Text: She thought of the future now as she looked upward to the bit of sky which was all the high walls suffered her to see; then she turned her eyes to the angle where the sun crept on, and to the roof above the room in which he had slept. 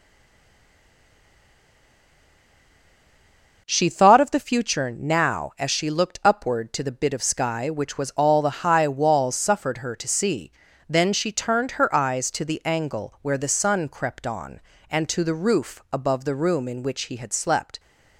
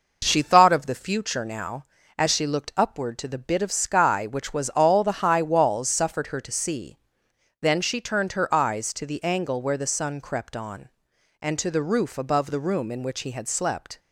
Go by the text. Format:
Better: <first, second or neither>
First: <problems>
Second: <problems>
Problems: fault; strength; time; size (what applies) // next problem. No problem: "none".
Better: second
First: stays silent before the first word; strong; until 3.6 s; 3.6 s long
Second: none